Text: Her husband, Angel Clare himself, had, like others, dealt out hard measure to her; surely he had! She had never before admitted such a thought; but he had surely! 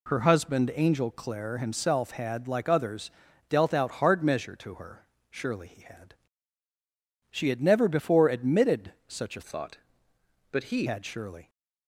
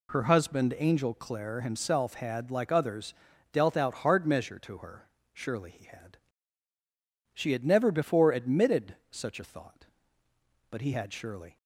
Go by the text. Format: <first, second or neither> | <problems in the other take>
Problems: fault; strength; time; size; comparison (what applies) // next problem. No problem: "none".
second | pauses between "admitted" and "such"; slight; at 8.9 s; 0.16 s long; slight in the second // changes voice from "thought" to "he"; from 9.4 to 10.8 s; 1.4 s long